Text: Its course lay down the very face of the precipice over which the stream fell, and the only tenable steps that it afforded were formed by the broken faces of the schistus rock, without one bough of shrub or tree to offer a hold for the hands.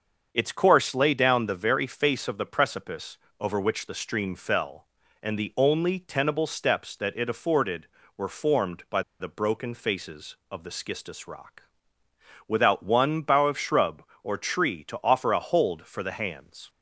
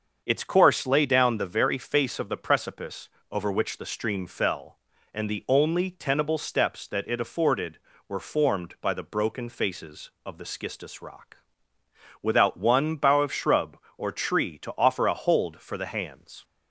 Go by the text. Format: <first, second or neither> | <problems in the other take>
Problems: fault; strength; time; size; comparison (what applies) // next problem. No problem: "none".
second | starts louder than the rest; until 1.3 s; 6.5 dB; also in the second // pauses between "precipice" and "over"; slight; at 3.1 s; 0.24 s long; slight in the second // pauses between "by" and "the"; slight; at 9.0 s; 0.19 s long